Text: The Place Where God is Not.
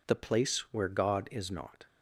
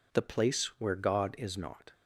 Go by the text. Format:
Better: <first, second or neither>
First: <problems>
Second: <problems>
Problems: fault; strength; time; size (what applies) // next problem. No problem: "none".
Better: neither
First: none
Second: none